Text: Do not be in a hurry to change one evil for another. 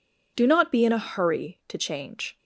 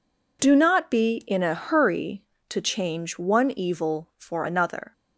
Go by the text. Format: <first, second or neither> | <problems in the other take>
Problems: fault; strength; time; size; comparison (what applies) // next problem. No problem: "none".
second | stops before "one evil for another"; at 2.3 s